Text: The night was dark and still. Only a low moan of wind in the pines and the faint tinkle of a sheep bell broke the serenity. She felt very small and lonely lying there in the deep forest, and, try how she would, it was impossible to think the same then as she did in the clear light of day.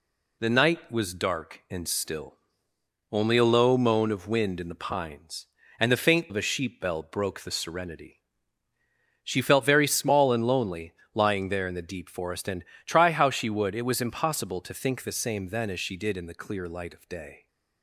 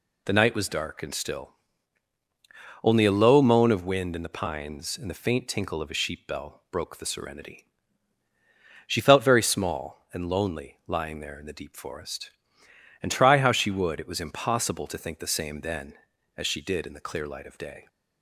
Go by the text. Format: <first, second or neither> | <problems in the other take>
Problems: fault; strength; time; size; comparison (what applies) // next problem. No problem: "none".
second | skips "tinkle"; at 6.2 s // pauses between "lonely" and "lying"; slight; at 10.9 s; 0.22 s long